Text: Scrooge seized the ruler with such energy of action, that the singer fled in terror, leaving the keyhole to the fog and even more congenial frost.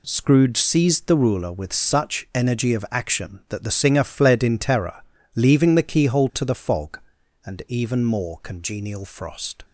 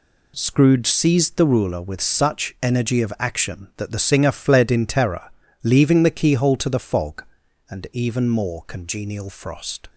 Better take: neither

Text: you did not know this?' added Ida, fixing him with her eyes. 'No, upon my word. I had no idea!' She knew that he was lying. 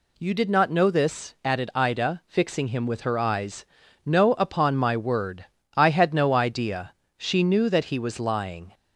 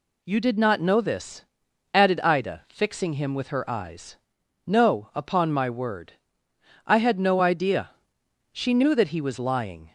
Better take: neither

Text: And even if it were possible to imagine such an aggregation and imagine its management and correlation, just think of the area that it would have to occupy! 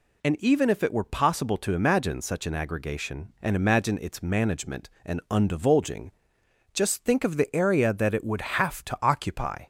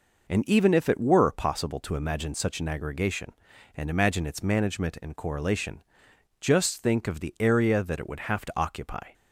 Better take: second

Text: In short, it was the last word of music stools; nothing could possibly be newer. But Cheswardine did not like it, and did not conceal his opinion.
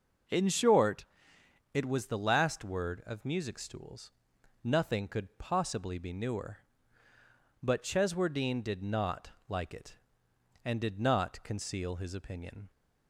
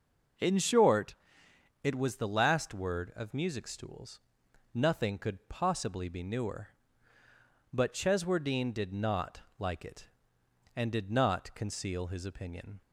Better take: neither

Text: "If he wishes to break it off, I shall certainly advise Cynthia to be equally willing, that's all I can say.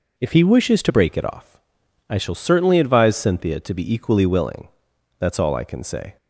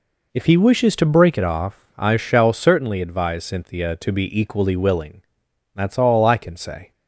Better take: second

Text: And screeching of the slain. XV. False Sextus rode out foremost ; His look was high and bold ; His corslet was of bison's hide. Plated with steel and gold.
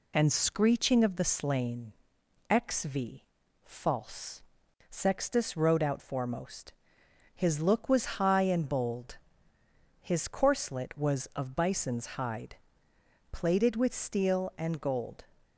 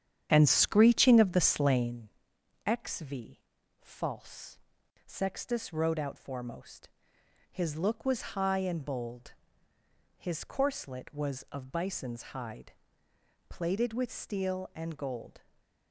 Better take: first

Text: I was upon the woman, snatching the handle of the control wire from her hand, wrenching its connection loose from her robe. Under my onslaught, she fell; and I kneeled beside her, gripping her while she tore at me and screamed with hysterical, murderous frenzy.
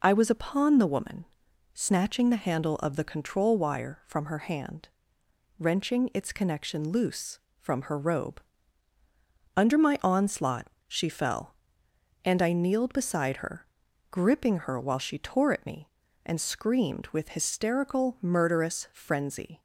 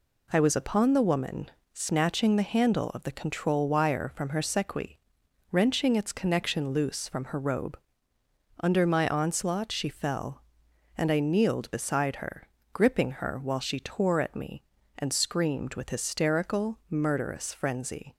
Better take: first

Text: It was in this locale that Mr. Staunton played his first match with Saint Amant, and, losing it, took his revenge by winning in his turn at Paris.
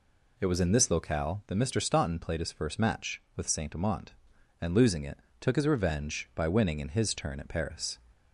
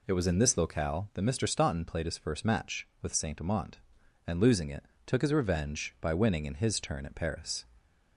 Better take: neither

